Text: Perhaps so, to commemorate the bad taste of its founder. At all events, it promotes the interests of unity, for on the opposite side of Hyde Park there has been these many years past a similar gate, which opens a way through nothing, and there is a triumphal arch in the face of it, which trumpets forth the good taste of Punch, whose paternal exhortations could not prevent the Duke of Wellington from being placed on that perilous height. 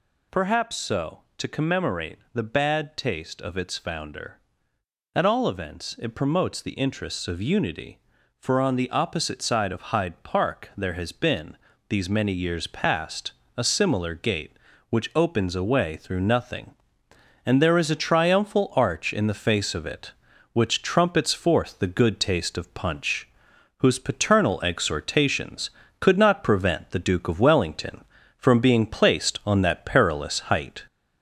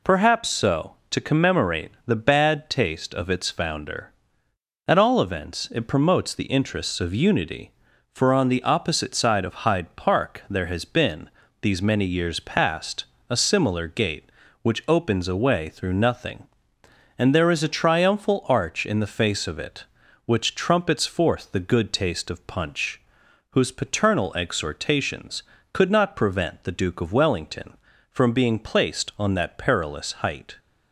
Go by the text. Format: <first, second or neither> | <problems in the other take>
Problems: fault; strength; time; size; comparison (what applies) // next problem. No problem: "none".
second | gets louder; throughout; 3.5 dB // pauses between "commemorate" and "the"; slight; at 2.1 s; 0.16 s long; slight in the second // pauses between "been" and "these"; slight; at 11.5 s; 0.32 s long; slight in the second // pauses between "past" and "a"; slight; at 13.3 s; 0.24 s long; slight in the second